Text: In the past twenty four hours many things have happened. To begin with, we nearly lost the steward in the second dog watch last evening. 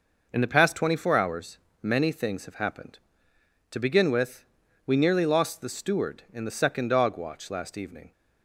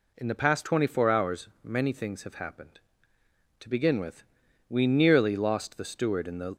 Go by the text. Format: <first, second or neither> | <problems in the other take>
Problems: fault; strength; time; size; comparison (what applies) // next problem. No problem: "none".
first | pauses between "hours" and "many"; slight; at 1.4 s; 0.16 s long; slight in the first // stops before "second dog watch last evening"; at 6.5 s